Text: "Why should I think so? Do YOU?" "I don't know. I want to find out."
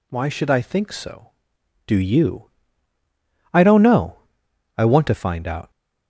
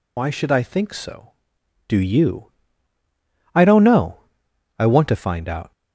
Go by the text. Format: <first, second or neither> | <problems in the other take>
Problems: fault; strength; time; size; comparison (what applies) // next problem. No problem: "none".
first | loses the start of "Why"; at 0.1 s; 55 ms